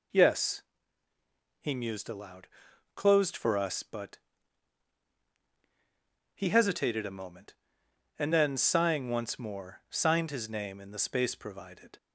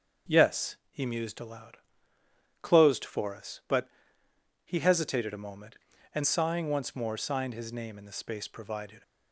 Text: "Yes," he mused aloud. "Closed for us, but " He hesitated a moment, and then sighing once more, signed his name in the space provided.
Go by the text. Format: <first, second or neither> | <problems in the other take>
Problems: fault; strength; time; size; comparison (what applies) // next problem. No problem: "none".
first | skips "then"; at 6.2 s